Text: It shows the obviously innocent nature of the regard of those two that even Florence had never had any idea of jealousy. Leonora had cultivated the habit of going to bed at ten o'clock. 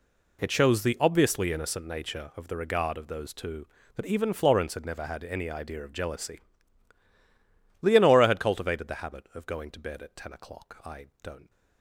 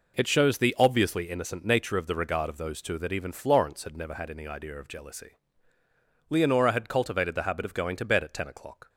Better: second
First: goes on to say "I don't"; noticeable; from 10.8 s on; 0.66 s long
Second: none

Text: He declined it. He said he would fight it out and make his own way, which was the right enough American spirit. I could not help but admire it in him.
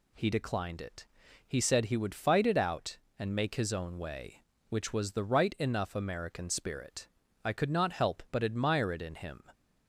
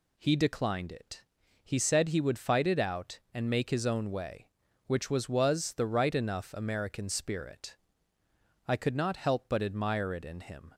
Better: first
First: none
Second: says "was" twice; at 5.2 s

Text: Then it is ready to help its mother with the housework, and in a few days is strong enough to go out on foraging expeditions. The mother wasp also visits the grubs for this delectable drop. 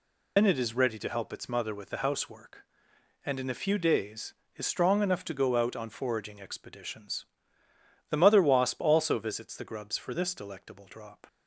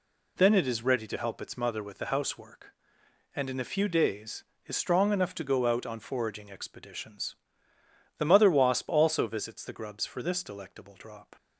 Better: second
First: loses the start of "Then"; at 0.3 s; 70 ms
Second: none

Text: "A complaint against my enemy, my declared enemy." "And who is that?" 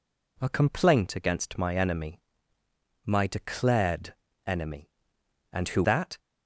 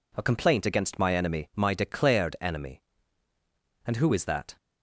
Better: second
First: pauses between "declared" and "enemy"; slight; at 4.1 s; 0.32 s long // skips "is"; at 5.8 s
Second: none

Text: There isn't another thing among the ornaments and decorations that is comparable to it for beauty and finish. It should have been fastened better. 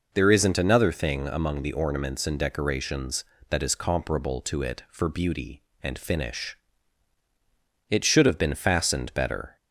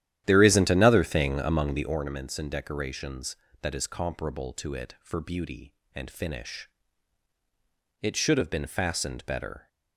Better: first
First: none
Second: starts louder than the rest; strong; until 2.1 s; 11.5 dB

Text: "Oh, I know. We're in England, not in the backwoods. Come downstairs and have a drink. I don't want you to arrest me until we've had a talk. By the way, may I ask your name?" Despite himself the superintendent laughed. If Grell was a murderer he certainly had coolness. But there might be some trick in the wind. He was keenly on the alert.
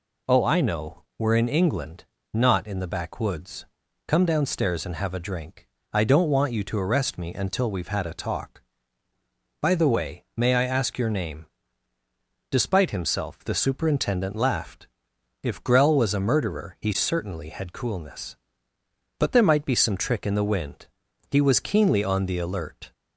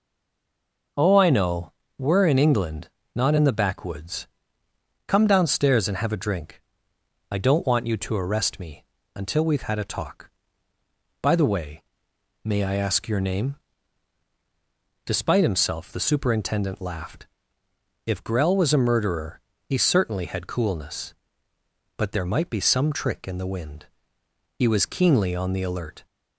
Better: first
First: none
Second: stays silent before the first word; slight; until 0.9 s; 0.9 s long // pauses between "me" and "until"; slight; at 8.8 s; 0.32 s long // pauses between "murderer" and "he"; slight; at 19.4 s; 0.26 s long

